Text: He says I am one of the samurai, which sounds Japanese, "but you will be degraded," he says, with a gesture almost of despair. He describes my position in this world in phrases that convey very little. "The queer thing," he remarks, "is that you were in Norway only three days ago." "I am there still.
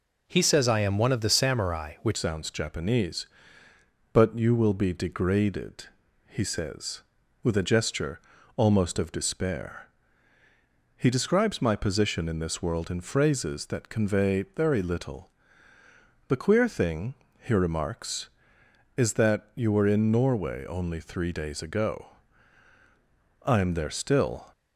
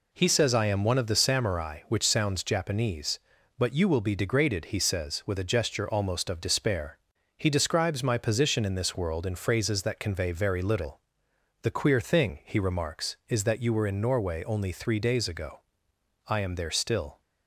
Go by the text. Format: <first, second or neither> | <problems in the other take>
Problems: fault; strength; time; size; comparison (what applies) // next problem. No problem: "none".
second | changes voice at "sounds"; from 2.1 s on; 22.4 s long // pauses between "gesture" and "almost"; slight; at 8.1 s; 0.36 s long